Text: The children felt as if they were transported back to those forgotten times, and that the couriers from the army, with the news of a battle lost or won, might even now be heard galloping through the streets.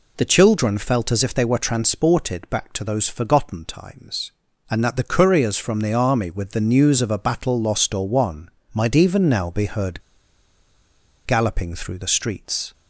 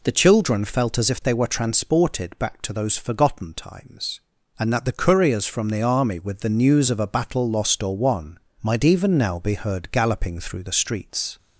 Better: second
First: pauses between "heard" and "galloping"; strong; at 10.0 s; 1.2 s long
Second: none

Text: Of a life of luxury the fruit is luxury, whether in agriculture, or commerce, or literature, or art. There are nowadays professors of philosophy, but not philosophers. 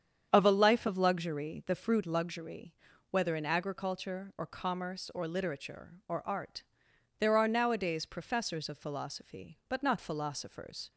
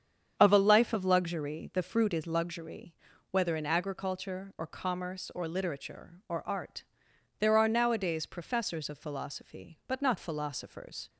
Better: second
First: starts louder than the rest; strong; until 1.3 s; 8 dB // skips "is"; at 2.0 s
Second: starts louder than the rest; strong; until 1.3 s; 8 dB

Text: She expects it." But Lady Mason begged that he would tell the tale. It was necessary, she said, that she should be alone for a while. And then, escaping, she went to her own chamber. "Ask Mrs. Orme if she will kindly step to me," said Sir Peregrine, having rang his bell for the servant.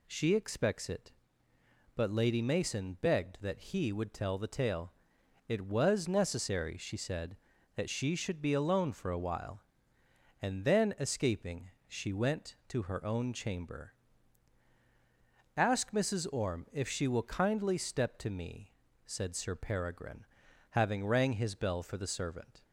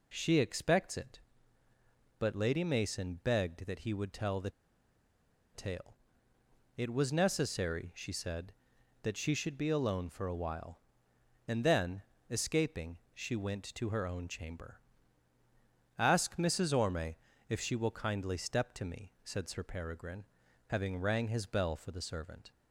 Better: first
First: none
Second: pauses between "the" and "tale"; at 4.5 s; 1.0 s long // pauses between "Orme" and "if"; slight; at 17.1 s; 0.32 s long

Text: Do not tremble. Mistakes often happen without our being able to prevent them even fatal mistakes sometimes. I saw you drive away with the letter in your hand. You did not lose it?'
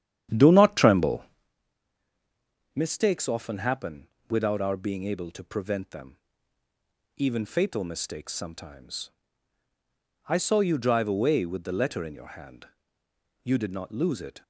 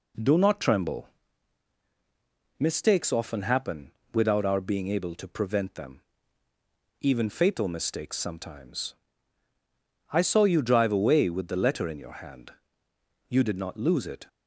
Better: second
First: starts louder than the rest; strong; until 1.5 s; 10 dB // pauses between "happen" and "without"; slight; at 4.0 s; 0.24 s long // pauses between "them" and "even"; noticeable; at 6.1 s; 0.98 s long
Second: pauses between "happen" and "without"; slight; at 3.8 s; 0.24 s long // pauses between "them" and "even"; noticeable; at 6.0 s; 0.98 s long

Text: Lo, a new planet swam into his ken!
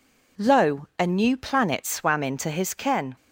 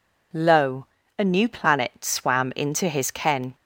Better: neither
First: none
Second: none

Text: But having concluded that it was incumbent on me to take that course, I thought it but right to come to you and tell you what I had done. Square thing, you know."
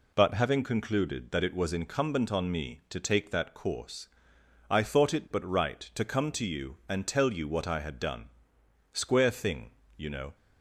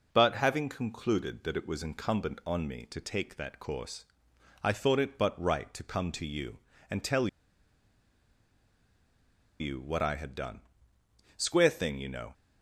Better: first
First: none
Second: pauses between "tell" and "you"; strong; at 7.2 s; 2.3 s long

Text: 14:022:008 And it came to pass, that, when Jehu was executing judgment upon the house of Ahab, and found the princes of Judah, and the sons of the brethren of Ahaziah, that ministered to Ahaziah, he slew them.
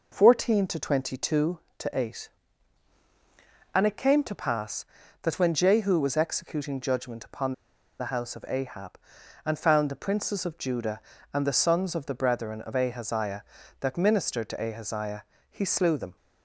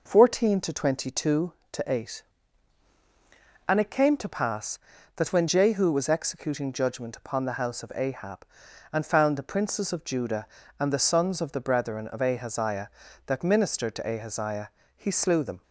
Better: second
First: pauses between "upon" and "the"; noticeable; at 7.5 s; 0.46 s long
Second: none

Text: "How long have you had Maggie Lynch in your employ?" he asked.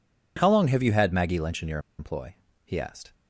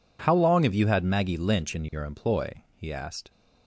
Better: second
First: pauses between "your" and "employ"; slight; at 1.7 s; 0.19 s long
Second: none

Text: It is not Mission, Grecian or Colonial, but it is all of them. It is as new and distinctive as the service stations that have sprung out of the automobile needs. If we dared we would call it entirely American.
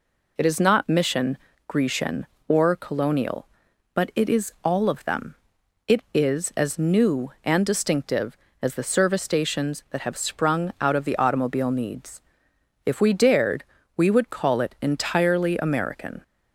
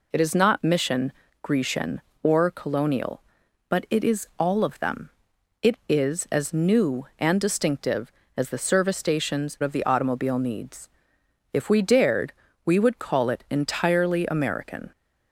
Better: first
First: pauses between "dared" and "we"; slight; at 13.6 s; 0.30 s long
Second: skips "that have sprung out"; at 9.5 s // pauses between "dared" and "we"; slight; at 12.3 s; 0.30 s long

